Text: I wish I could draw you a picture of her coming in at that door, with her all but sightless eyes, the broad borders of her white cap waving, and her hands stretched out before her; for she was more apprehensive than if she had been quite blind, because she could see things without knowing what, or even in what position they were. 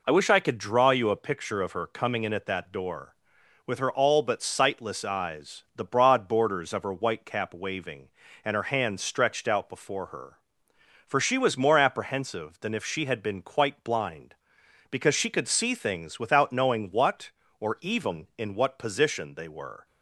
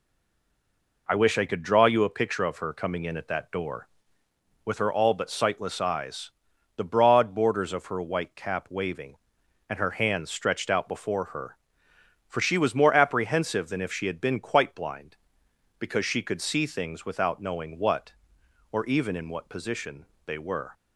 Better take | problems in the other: first | stays silent before the first word; until 1.0 s; 1.0 s long // pauses between "position" and "they"; slight; at 20.0 s; 0.20 s long

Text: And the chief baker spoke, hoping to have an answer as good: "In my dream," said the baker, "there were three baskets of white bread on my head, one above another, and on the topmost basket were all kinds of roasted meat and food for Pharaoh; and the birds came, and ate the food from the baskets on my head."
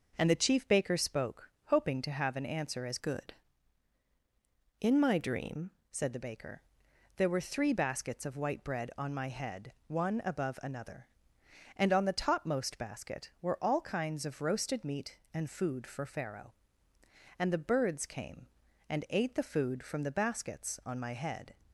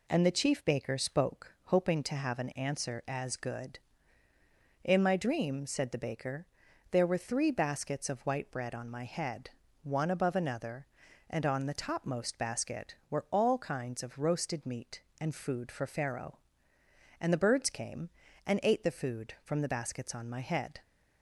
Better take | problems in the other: second | changes voice from "good" to "dream"; from 2.9 to 5.7 s; 2.8 s long

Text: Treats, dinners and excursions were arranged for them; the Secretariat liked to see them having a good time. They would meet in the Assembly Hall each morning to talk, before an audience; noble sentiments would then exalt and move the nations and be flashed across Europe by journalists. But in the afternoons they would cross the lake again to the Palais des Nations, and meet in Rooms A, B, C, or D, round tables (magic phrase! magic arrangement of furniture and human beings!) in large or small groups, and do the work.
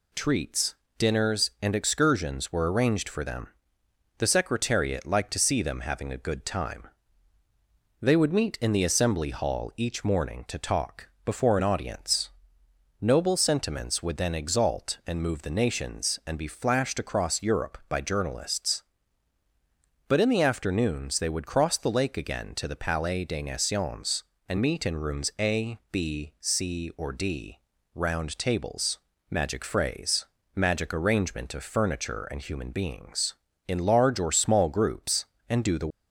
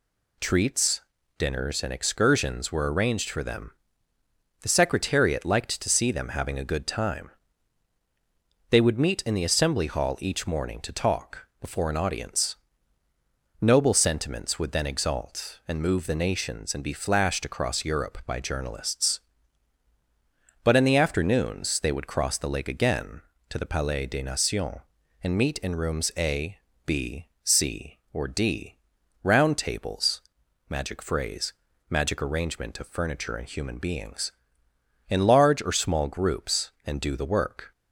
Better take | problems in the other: second | stops before "work"; at 35.9 s

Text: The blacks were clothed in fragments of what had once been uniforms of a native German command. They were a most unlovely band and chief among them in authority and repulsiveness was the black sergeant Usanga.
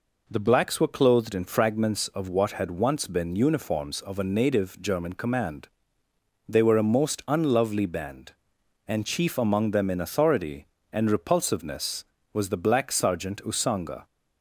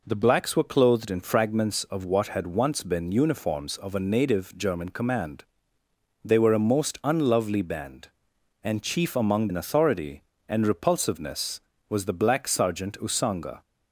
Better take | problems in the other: first | skips "them"; at 9.4 s

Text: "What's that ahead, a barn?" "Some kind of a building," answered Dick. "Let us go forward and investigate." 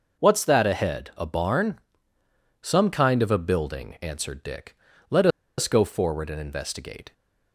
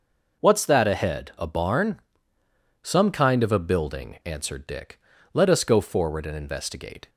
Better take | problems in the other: second | pauses between "Let" and "us"; slight; at 5.2 s; 0.30 s long

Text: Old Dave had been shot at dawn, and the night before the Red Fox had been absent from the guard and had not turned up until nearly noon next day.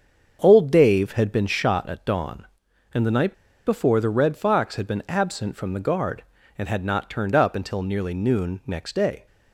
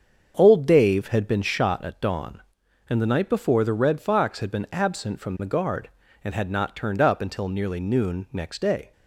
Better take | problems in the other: second | starts louder than the rest; until 1.4 s; 7 dB; strong in the second // pauses between "night" and "before"; slight; at 3.3 s; 0.32 s long

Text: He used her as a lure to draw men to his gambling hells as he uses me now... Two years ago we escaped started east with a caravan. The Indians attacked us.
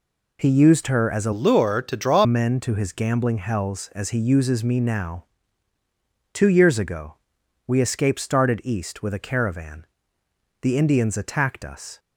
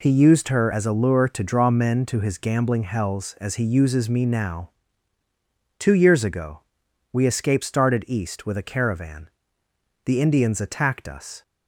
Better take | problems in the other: second | changes voice from "lure" to "draw"; from 1.3 to 2.2 s; 0.9 s long // pauses between "ago" and "we"; noticeable; at 7.1 s; 0.52 s long; noticeable in the second

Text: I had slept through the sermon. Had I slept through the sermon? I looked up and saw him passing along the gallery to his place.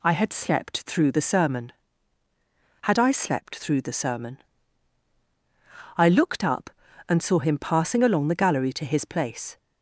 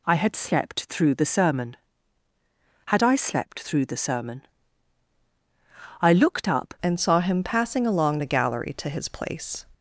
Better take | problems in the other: first | changes voice at "and"; from 6.8 s on; 2.8 s long

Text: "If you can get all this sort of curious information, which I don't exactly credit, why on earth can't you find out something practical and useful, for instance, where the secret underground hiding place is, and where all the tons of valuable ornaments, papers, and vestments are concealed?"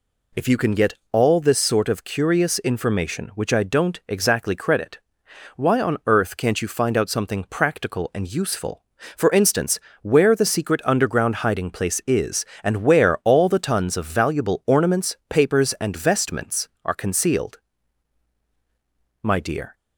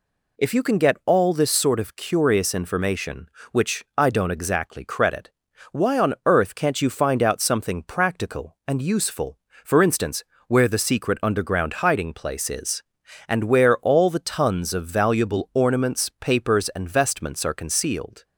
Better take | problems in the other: second | pauses between "get" and "all"; slight; at 0.9 s; 0.16 s long // goes on to say "My dear"; from 19.2 s on; 0.52 s long

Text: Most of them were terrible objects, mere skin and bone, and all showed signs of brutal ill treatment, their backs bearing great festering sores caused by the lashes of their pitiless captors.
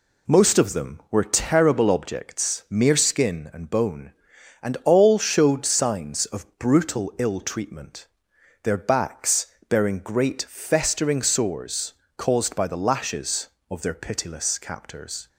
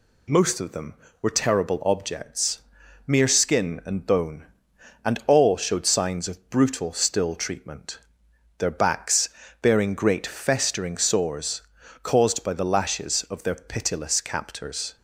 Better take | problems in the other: first | says "still" for "ill"; at 6.9 s // pauses between "backs" and "bearing"; slight; at 9.3 s; 0.32 s long; slight in the first // pauses between "sores" and "caused"; at 11.6 s; 0.40 s long; slight in the first

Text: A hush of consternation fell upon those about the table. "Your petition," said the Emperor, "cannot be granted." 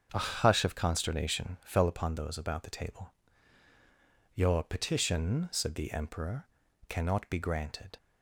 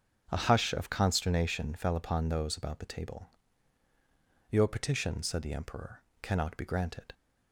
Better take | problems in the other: neither | starts louder than the rest; the same in both

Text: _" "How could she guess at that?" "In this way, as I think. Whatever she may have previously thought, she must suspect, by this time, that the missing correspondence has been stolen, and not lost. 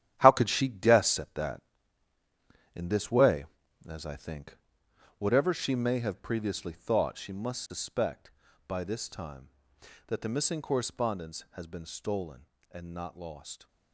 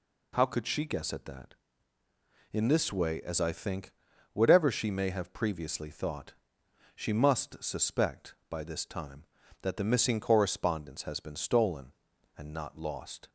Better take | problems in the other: second | gets quieter; strong; throughout; 10 dB

